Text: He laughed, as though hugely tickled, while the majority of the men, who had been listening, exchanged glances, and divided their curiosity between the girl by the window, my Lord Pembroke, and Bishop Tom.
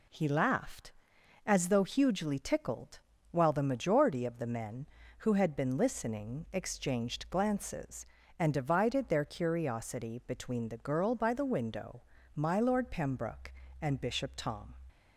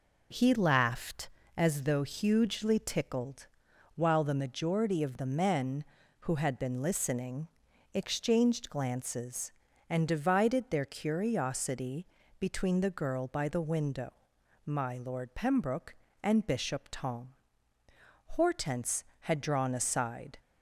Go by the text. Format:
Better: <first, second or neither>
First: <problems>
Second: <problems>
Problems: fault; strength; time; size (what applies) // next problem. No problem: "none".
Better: first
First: none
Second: pauses between "curiosity" and "between"; slight; at 12.0 s; 0.34 s long // goes on to say "Hortense had drawn aside"; strong; from 18.2 s on; 2.0 s long